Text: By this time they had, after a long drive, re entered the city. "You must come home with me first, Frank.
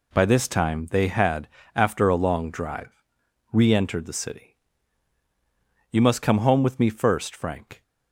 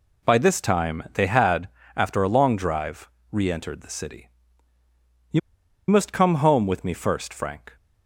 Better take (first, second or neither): first